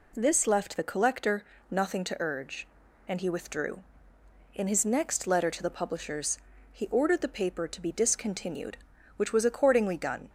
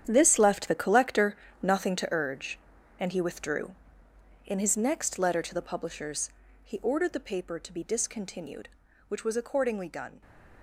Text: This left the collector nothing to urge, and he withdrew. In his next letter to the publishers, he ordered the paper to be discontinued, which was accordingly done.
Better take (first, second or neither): first